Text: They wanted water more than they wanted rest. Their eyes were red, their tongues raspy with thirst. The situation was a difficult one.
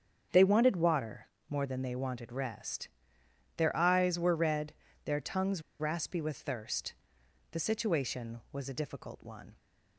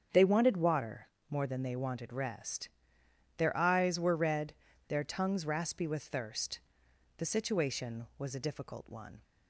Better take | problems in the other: second | starts louder than the rest; strong; until 1.5 s; 7.5 dB; strong in the second // pauses between "water" and "more"; slight; at 1.2 s; 0.22 s long; slight in the second // pauses between "tongues" and "raspy"; slight; at 5.6 s; 0.18 s long

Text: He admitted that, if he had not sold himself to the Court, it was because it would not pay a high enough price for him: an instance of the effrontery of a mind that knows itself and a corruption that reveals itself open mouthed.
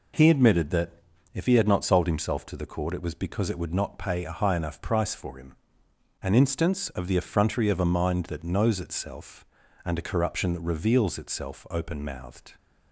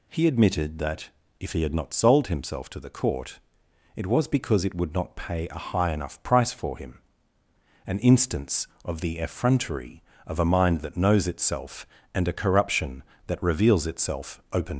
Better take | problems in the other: first | stops before "mouthed"; at 14.7 s

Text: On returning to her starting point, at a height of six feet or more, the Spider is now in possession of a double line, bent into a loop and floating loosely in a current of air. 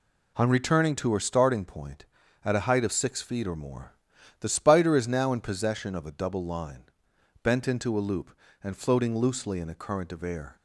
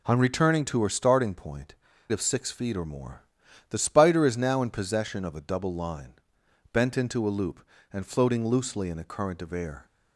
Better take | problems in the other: first | skips "at a height"; at 1.9 s

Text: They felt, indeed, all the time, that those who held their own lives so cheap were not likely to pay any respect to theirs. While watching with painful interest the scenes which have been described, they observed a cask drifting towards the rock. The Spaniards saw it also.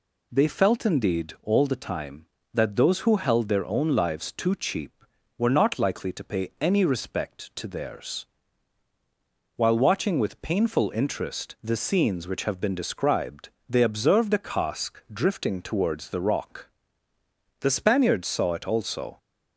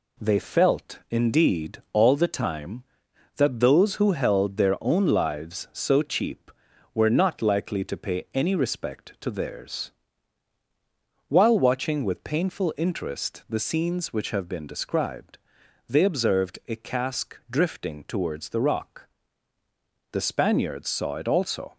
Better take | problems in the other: second | says "too" for "so"; at 4.3 s

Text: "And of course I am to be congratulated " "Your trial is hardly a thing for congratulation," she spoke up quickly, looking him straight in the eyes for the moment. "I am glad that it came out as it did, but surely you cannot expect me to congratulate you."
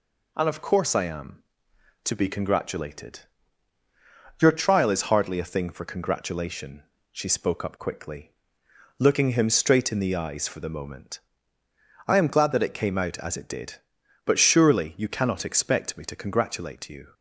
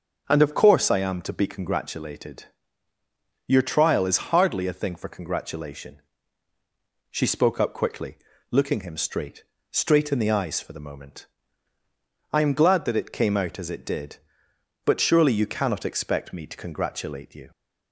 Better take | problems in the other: first | says "straight" twice; at 9.6 s

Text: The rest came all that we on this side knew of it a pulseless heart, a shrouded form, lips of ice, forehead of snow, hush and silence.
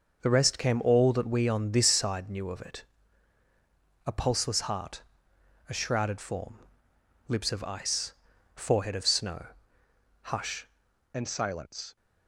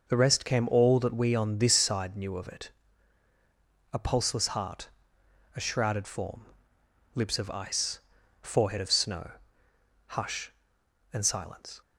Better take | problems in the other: second | pauses between "it" and "a"; at 2.8 s; 1.2 s long; also in the second // changes voice at "and"; from 11.1 s on; 0.8 s long

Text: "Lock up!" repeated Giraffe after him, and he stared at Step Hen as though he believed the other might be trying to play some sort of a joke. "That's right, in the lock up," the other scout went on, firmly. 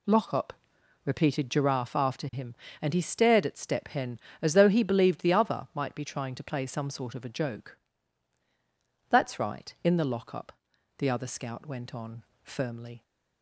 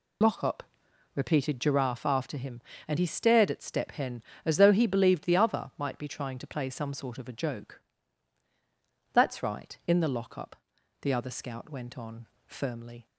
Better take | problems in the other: first | loses the start of "Lock"; at 0.2 s; 45 ms

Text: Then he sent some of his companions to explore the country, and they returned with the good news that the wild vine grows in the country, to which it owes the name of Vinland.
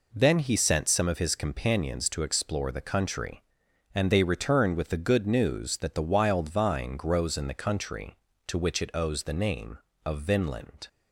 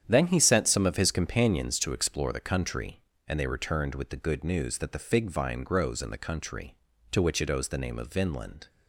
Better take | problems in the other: first | starts louder than the rest; strong; until 1.0 s; 9.5 dB // says "fig" for "wild"; at 4.9 s

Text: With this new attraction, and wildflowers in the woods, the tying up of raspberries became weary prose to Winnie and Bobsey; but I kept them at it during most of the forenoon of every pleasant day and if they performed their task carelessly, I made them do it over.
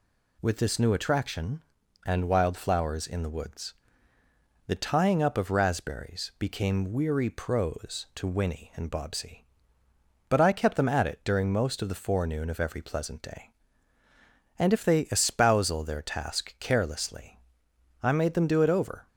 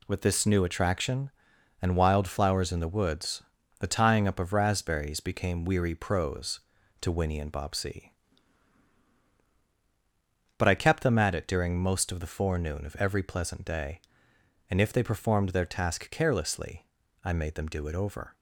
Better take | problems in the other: second | says "espousal" for "performed"; at 15.0 s

